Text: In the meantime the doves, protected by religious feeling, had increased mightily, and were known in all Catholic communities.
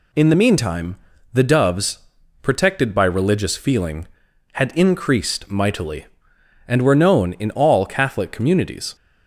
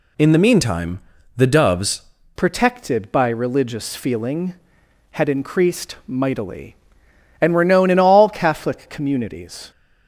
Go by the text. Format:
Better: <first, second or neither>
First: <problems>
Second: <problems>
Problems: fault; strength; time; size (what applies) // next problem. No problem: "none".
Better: first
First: pauses between "meantime" and "the"; slight; at 0.9 s; 0.34 s long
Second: pauses between "meantime" and "the"; slight; at 1.0 s; 0.34 s long // changes voice at "protected"; from 2.3 s on; 7.4 s long